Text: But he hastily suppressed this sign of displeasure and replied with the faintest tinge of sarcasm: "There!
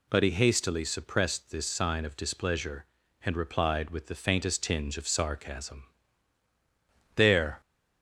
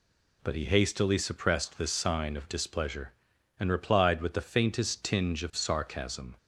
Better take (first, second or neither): first